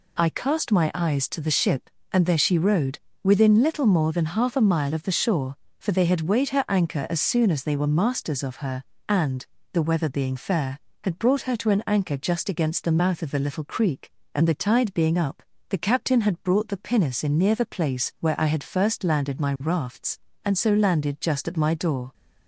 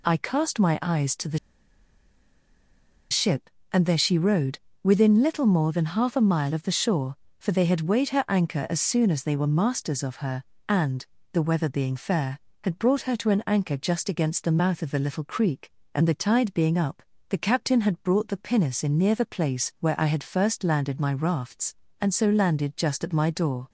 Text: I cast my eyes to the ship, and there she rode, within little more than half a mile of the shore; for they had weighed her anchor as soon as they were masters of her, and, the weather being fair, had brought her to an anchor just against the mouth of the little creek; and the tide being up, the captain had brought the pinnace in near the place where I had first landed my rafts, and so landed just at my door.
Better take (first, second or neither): first